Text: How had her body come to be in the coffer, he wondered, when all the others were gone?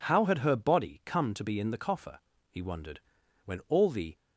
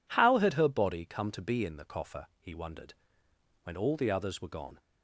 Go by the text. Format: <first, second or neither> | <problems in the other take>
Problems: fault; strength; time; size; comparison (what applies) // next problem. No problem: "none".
second | stops before "others were gone"; at 4.1 s